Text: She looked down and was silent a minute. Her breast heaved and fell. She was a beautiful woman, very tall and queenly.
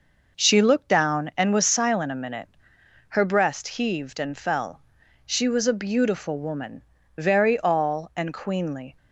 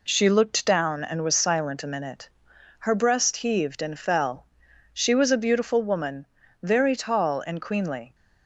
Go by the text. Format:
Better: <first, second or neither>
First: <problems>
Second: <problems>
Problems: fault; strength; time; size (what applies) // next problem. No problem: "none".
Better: second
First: says "all" for "tall"; at 7.6 s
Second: none